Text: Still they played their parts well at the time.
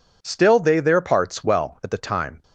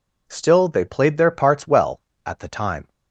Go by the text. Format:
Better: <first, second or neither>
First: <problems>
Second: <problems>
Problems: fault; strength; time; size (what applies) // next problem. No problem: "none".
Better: second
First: skips "played"; at 0.8 s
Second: none